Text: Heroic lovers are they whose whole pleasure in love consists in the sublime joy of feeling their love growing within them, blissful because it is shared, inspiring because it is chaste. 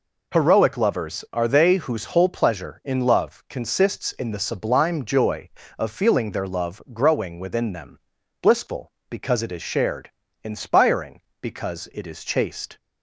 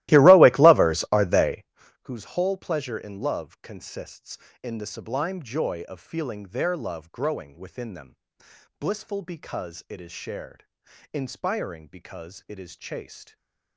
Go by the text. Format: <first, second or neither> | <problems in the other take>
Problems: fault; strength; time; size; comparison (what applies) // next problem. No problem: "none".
first | starts louder than the rest; strong; until 1.7 s; 16.5 dB // pauses between "they" and "whose"; slight; at 1.6 s; 0.36 s long // stays silent after the last word; slight; from 13.2 s on; 0.5 s long